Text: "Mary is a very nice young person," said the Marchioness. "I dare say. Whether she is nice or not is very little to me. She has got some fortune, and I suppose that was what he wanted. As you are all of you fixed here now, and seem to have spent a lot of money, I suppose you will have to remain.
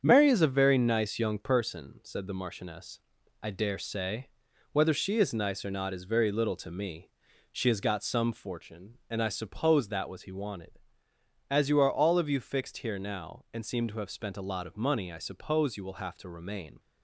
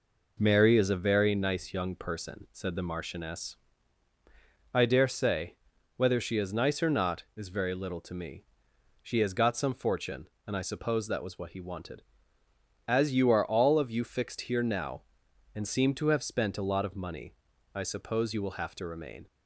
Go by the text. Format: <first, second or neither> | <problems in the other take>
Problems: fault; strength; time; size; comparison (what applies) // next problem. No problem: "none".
second | starts louder than the rest; strong; until 1.0 s; 7.5 dB // skips "what"; at 10.2 s